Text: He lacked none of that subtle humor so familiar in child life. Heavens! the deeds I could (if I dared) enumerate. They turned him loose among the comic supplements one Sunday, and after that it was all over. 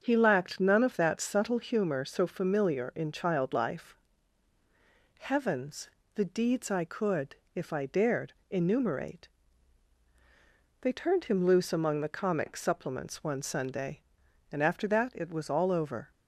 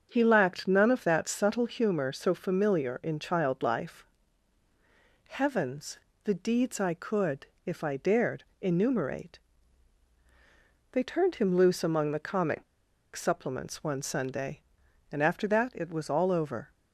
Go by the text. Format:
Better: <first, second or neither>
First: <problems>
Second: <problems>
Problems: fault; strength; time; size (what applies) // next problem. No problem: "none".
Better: first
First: starts louder than the rest; until 1.0 s; 7 dB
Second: starts louder than the rest; until 1.1 s; 7 dB // pauses between "comic" and "supplements"; noticeable; at 12.6 s; 0.50 s long